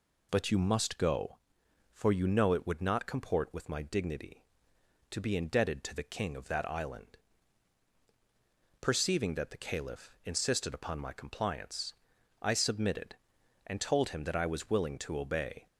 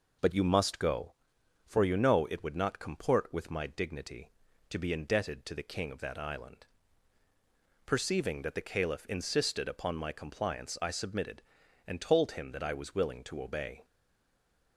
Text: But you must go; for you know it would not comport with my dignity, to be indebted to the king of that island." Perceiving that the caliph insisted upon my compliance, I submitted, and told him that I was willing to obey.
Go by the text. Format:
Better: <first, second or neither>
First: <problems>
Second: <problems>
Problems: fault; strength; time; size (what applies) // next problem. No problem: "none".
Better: first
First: none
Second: stays silent after the last word; slight; from 13.8 s on; 0.9 s long